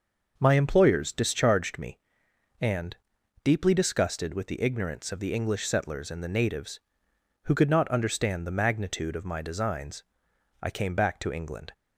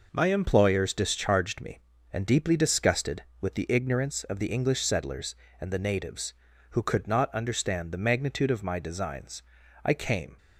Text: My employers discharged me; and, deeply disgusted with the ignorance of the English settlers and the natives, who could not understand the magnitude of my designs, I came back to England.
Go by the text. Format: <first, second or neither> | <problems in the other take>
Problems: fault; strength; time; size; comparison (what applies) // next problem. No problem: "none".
first | stops before "back to England"; at 10.3 s